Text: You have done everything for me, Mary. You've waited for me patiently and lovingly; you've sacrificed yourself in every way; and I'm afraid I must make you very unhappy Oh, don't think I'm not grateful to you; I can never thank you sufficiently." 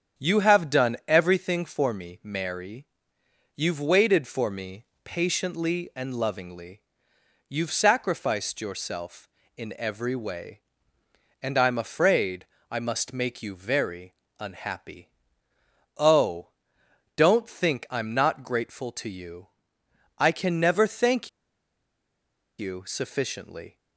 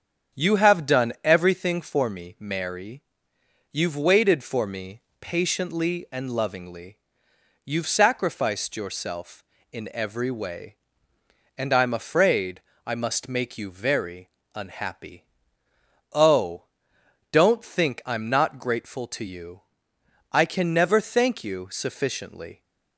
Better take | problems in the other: second | starts louder than the rest; strong; until 1.2 s; 7.5 dB; strong in the second // pauses between "me" and "patiently"; slight; at 4.8 s; 0.18 s long; slight in the second // pauses between "afraid" and "I"; slight; at 12.4 s; 0.24 s long; slight in the second // pauses between "very" and "unhappy"; slight; at 14.1 s; 0.24 s long; slight in the second // pauses between "unhappy" and "Oh"; noticeable; at 15.1 s; 0.88 s long; noticeable in the second // pauses between "thank" and "you"; strong; at 21.2 s; 1.3 s long

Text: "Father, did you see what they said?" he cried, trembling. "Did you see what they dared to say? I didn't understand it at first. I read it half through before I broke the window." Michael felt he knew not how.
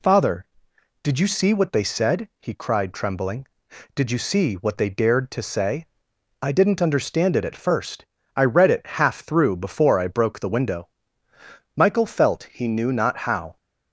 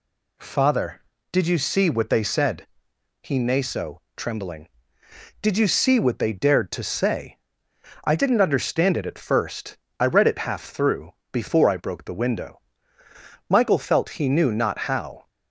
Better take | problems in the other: first | says "naso" for "cried"; at 3.3 s // pauses between "through" and "before"; slight; at 11.1 s; 0.20 s long

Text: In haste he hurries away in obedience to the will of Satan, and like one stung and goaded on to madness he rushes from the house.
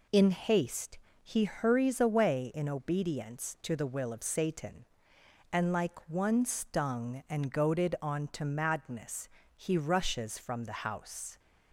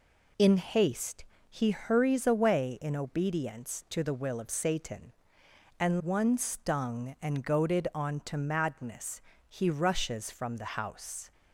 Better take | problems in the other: first | pauses between "haste" and "he"; slight; at 1.2 s; 0.24 s long; slight in the first // skips "like"; at 6.0 s // pauses between "madness" and "he"; slight; at 9.1 s; 0.30 s long; slight in the first

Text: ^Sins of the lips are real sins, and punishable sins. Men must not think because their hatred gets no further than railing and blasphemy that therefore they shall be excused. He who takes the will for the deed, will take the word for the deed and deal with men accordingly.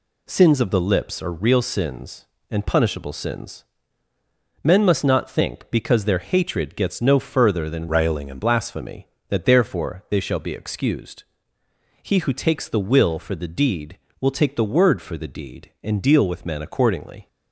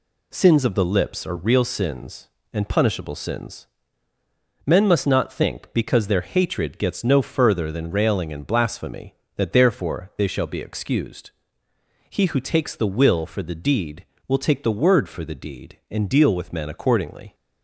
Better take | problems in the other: second | changes voice from "railing" to "and"; from 7.8 to 8.4 s; 0.6 s long

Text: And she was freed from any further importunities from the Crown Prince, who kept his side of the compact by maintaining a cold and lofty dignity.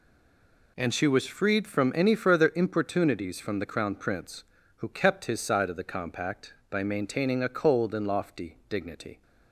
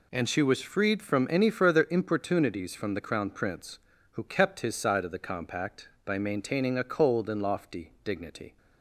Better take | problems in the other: second | stays silent before the first word; slight; until 0.7 s; 0.7 s long

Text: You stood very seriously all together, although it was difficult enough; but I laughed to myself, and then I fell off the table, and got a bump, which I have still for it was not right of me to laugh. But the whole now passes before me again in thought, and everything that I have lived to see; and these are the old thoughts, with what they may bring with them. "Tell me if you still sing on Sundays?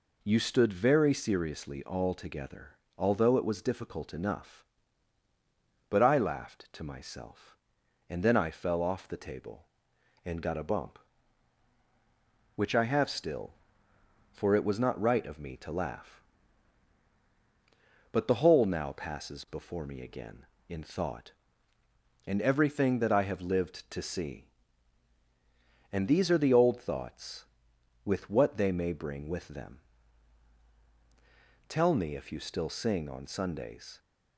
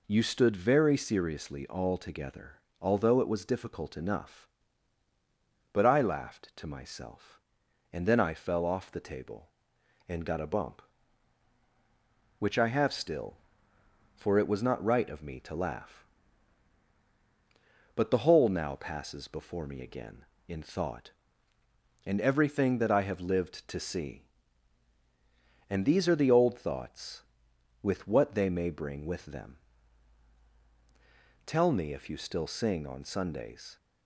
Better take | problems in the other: neither | none

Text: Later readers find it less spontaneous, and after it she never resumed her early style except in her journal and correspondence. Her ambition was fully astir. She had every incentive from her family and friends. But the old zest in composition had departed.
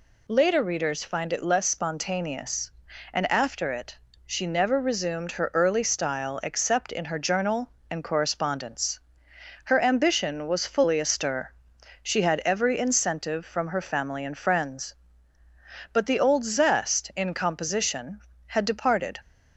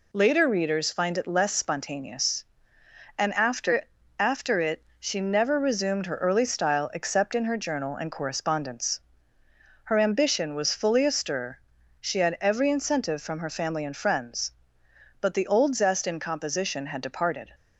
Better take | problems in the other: first | says "after" twice; at 4.1 s // pauses between "it" and "she"; slight; at 4.8 s; 0.18 s long; slight in the first

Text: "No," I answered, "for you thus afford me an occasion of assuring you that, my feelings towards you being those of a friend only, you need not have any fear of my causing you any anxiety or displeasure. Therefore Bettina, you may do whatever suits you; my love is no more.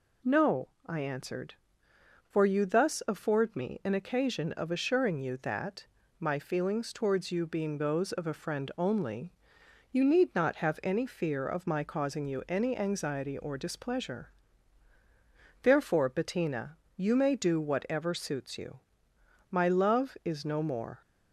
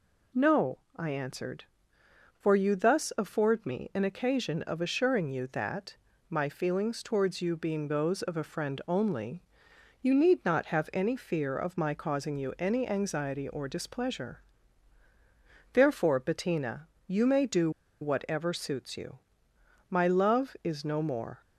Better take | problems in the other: first | pauses between "do" and "whatever"; slight; at 17.7 s; 0.31 s long

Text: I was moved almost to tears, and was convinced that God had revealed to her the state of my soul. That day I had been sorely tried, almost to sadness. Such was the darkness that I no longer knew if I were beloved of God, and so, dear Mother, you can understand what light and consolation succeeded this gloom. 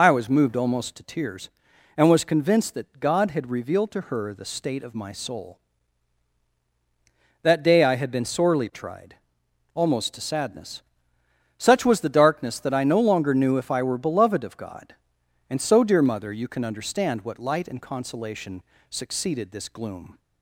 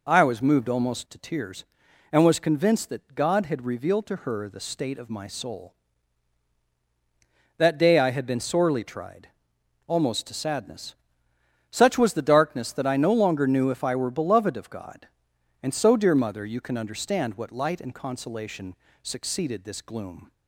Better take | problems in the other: second | loses the start of "I"; at 0.0 s; 60 ms // pauses between "consolation" and "succeeded"; slight; at 18.6 s; 0.30 s long; slight in the second

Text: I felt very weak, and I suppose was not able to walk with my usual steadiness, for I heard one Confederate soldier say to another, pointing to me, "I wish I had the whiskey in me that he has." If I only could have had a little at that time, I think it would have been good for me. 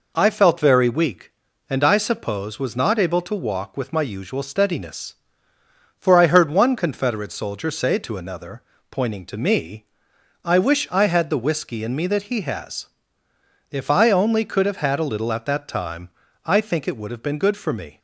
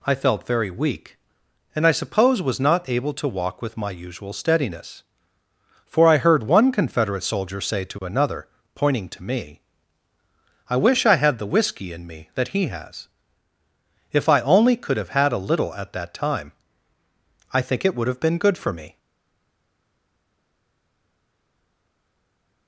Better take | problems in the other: first | stays silent after the last word; strong; from 18.9 s on; 3.7 s long

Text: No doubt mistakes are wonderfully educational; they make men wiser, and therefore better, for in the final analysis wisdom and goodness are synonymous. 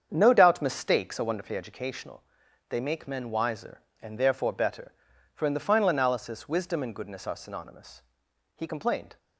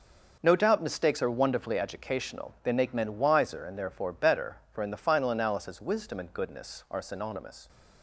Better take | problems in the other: second | starts louder than the rest; strong; until 1.1 s; 7.5 dB // goes on to say "He complained"; noticeable; from 8.5 s on; 0.62 s long

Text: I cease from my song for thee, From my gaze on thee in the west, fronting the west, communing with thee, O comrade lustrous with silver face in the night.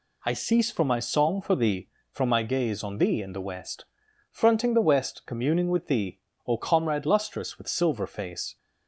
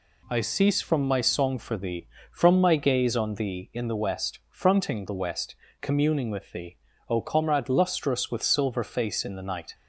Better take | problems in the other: second | stops before "in the night"; at 8.5 s

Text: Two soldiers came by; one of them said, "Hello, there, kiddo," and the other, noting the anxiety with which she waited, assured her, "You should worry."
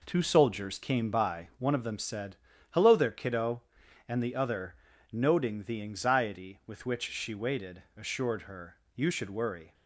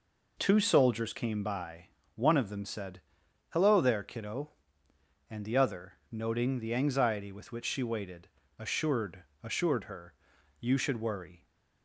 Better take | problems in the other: first | says "assured" twice; at 9.4 s

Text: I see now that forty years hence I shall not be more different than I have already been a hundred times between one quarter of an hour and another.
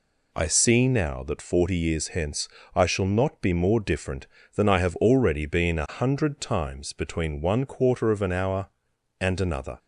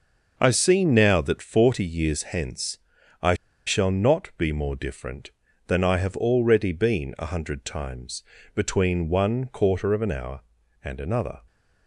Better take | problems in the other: first | starts louder than the rest; noticeable; until 1.3 s; 6 dB // pauses between "hence" and "I"; noticeable; at 2.7 s; 0.46 s long; slight in the first // pauses between "I" and "shall"; slight; at 3.3 s; 0.32 s long // pauses between "times" and "between"; slight; at 8.2 s; 0.32 s long

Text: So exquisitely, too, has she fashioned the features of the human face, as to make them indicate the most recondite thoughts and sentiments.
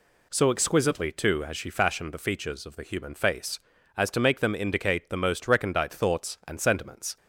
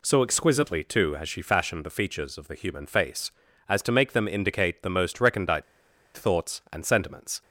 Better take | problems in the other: first | pauses between "recondite" and "thoughts"; noticeable; at 5.6 s; 0.53 s long

